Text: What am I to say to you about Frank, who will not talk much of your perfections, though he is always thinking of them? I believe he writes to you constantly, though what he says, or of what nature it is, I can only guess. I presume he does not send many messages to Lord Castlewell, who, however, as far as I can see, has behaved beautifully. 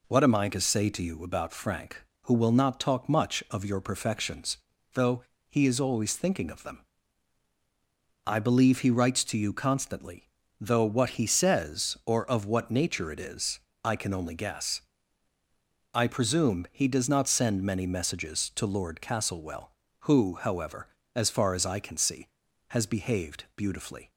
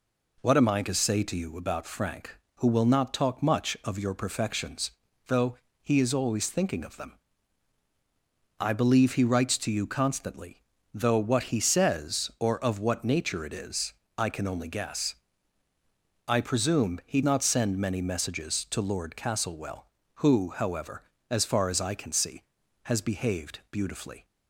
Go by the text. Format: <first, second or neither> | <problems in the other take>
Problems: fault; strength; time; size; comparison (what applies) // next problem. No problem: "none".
first | pauses between "though" and "he"; slight; at 5.5 s; 0.26 s long; slight in the first // skips "does"; at 17.2 s